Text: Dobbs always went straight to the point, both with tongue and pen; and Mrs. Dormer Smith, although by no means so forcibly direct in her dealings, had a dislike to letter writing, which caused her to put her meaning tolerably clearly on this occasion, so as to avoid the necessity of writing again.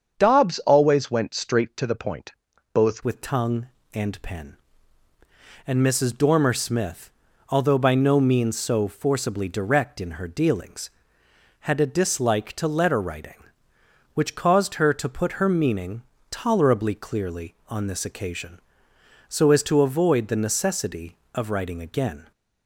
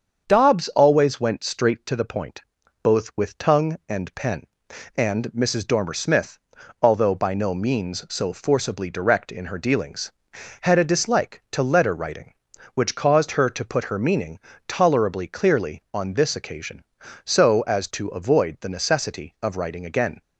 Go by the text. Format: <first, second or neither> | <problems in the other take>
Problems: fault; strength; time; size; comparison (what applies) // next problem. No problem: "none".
second | starts louder than the rest; strong; until 1.1 s; 7 dB; also in the second // changes voice at "with"; from 3.0 s on; 19.3 s long // pauses between "meaning" and "tolerably"; slight; at 16.0 s; 0.30 s long; slight in the second